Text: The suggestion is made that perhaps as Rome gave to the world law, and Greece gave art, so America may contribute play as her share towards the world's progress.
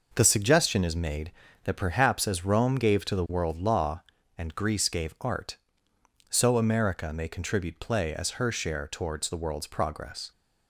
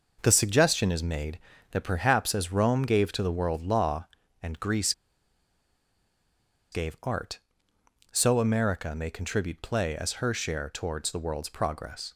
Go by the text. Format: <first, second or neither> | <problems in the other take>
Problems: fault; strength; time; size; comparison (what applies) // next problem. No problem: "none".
first | pauses between "Greece" and "gave"; strong; at 4.9 s; 1.8 s long